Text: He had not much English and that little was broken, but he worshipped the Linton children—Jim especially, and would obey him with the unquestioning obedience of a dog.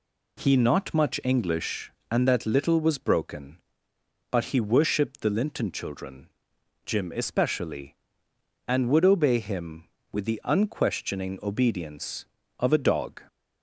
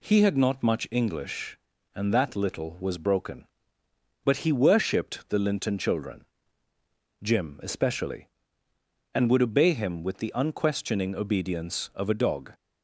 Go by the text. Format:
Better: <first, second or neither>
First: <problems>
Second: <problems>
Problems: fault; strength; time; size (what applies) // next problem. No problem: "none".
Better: second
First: skips "had"; at 0.5 s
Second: none